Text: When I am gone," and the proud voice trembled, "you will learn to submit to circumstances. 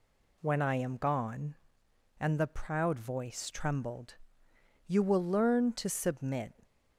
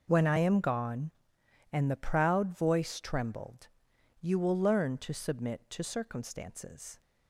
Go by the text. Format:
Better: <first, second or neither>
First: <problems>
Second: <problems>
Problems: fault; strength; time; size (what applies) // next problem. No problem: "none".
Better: second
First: stops before "to circumstances"; at 6.6 s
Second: none